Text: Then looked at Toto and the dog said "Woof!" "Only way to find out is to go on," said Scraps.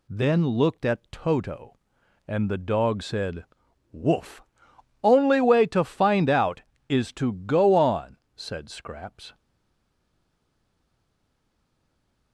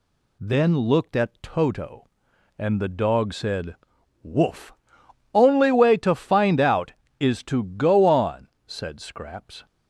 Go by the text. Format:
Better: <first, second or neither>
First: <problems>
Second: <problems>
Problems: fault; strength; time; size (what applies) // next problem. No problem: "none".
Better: second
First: pauses between "said" and "Woof"; noticeable; at 3.4 s; 0.48 s long // stays silent after the last word; strong; from 9.3 s on; 3.0 s long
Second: pauses between "said" and "Woof"; noticeable; at 3.7 s; 0.48 s long